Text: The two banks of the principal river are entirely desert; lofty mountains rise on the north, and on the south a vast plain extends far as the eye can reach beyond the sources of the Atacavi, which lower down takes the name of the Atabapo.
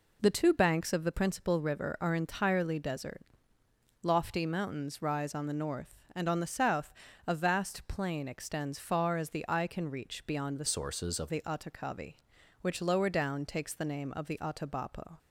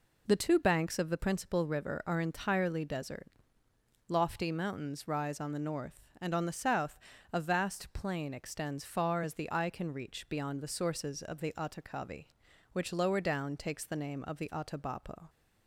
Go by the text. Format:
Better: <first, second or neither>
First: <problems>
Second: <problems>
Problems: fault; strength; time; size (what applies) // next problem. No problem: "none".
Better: second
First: pauses between "south" and "a"; slight; at 6.9 s; 0.34 s long // changes voice from "sources" to "of"; from 10.6 to 11.3 s; 0.7 s long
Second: pauses between "south" and "a"; slight; at 6.9 s; 0.34 s long